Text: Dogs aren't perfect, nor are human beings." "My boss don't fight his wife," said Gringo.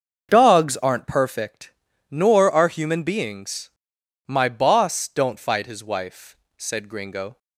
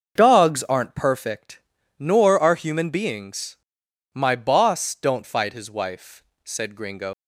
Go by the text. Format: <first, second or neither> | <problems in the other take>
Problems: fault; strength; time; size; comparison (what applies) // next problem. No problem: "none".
first | starts louder than the rest; until 1.1 s; 6.5 dB; also in the first // leaves "Gringo" unfinished; at 7.1 s; 115 ms